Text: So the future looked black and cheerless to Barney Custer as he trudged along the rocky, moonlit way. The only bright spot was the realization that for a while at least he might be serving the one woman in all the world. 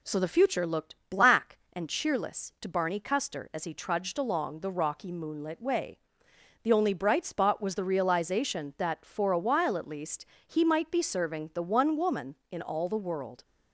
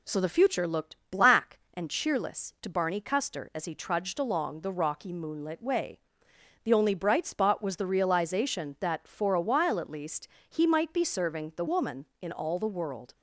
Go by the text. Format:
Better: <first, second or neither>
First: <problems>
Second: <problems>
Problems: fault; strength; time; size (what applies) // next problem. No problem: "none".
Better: first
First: pauses between "least" and "he"; slight; at 10.2 s; 0.22 s long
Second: pauses between "least" and "he"; slight; at 10.2 s; 0.22 s long // skips "one"; at 11.6 s